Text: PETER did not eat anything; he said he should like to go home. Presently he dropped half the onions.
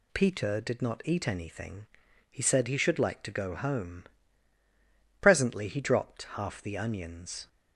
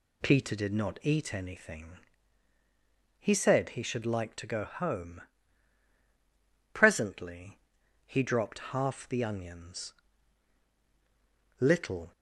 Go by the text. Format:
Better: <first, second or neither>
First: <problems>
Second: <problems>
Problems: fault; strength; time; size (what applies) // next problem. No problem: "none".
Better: first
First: none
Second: pauses between "Presently" and "he"; noticeable; at 7.5 s; 0.48 s long // goes on to say "LITTLE"; from 11.5 s on; 0.52 s long